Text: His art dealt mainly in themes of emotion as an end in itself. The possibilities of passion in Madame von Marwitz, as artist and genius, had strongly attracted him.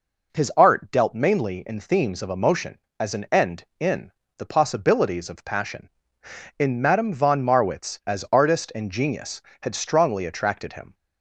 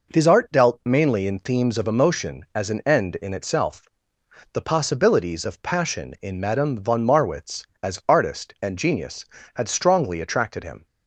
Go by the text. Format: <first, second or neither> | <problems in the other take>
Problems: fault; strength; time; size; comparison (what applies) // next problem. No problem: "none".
second | skips "itself"; at 4.2 s